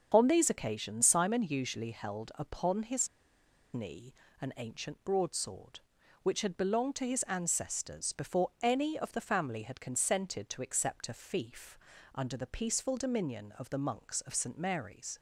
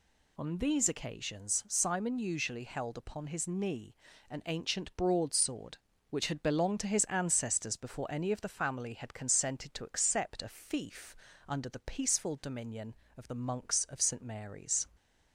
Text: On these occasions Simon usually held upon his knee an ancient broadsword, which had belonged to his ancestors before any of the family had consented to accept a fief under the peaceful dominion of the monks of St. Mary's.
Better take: second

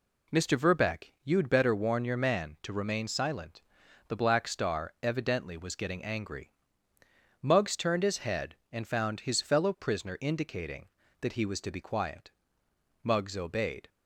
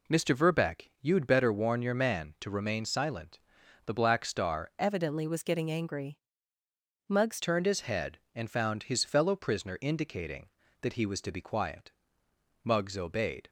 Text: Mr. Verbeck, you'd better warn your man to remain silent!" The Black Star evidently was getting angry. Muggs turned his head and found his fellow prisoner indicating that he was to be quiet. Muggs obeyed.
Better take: first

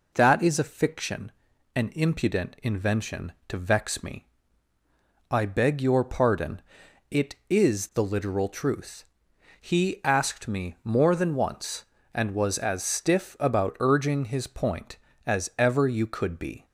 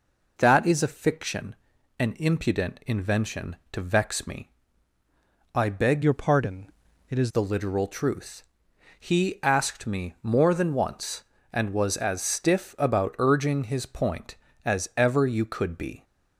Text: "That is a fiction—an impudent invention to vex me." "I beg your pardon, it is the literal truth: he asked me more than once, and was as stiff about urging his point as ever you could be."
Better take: first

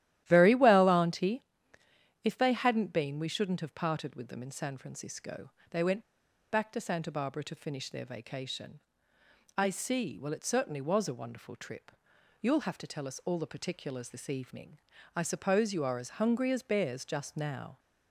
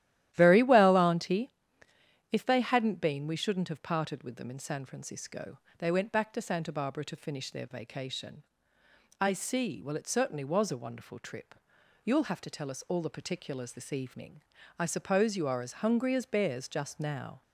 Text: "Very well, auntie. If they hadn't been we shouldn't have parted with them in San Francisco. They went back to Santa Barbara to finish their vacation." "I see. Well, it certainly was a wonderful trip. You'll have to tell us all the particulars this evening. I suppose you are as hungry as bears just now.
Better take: second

